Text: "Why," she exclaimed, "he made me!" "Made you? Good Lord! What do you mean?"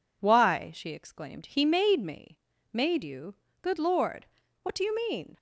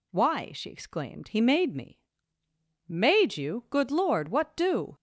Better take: first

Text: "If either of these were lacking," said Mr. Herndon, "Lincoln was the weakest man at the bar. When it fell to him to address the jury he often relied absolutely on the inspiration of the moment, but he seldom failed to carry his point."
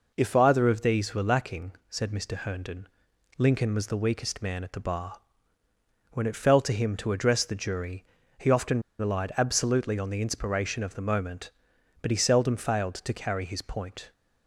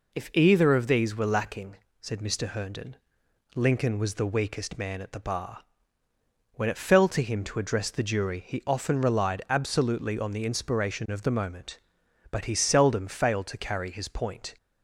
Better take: second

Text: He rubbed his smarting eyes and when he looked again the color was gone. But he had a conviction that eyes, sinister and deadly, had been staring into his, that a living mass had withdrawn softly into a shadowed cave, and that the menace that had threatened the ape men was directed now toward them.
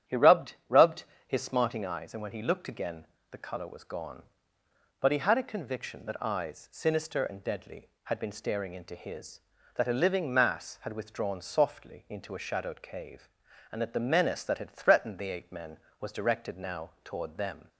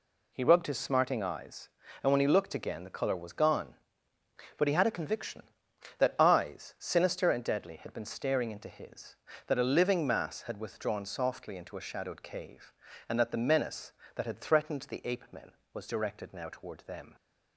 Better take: second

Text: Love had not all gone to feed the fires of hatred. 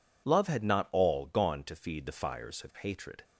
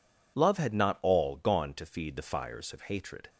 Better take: neither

